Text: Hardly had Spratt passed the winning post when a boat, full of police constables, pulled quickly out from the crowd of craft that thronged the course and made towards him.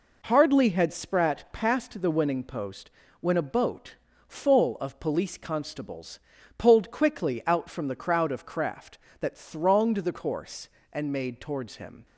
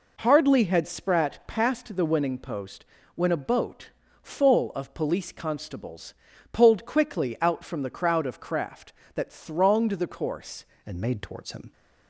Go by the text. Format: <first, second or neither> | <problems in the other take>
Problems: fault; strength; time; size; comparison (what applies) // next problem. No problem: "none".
first | pauses between "post" and "when"; slight; at 2.8 s; 0.30 s long; slight in the first // changes voice at "and"; from 10.8 s on; 0.9 s long